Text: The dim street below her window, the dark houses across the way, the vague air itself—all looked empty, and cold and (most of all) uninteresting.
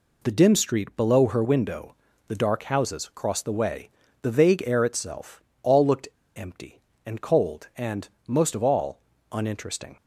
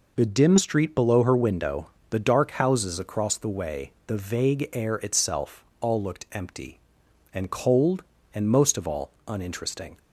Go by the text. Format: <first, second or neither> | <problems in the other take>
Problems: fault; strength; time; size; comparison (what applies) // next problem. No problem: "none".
second | pauses between "looked" and "empty"; slight; at 6.0 s; 0.29 s long